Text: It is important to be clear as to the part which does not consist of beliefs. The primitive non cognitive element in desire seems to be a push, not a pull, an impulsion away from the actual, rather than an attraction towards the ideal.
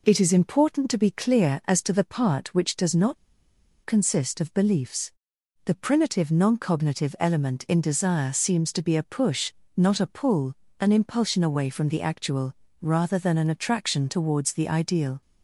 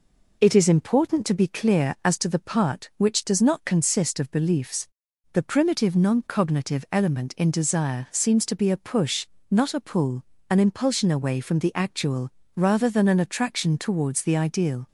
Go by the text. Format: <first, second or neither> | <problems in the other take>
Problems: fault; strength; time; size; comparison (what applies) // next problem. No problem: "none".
second | pauses between "not" and "consist"; noticeable; at 3.1 s; 0.69 s long